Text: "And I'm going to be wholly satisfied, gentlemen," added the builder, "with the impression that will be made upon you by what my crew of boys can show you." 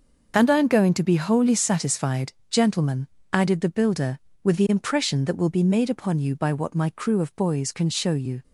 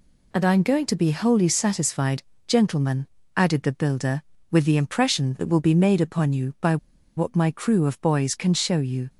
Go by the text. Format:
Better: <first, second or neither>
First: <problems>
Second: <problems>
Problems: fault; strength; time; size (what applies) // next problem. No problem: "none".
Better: first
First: none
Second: pauses between "by" and "what"; at 6.7 s; 0.40 s long